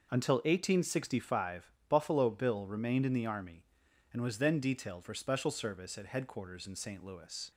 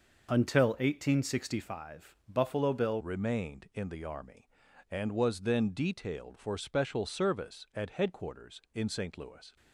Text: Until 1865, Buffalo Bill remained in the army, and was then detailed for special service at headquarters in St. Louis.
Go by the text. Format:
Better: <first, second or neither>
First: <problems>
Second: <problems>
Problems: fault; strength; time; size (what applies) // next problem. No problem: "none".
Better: first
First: none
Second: changes voice at "remained"; from 3.0 s on; 6.5 s long